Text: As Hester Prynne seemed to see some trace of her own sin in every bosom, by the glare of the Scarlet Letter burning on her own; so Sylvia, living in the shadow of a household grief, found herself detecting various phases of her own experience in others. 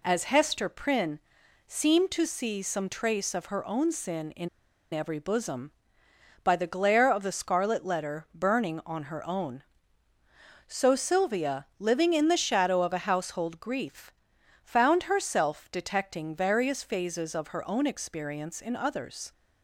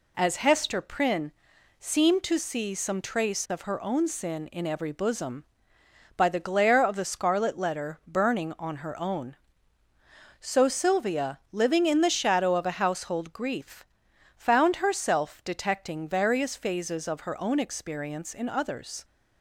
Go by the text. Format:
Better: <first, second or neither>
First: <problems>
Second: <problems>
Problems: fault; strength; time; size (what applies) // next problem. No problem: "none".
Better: second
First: pauses between "Prynne" and "seemed"; noticeable; at 1.2 s; 0.48 s long // pauses between "in" and "every"; at 4.4 s; 0.44 s long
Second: pauses between "Prynne" and "seemed"; noticeable; at 1.3 s; 0.48 s long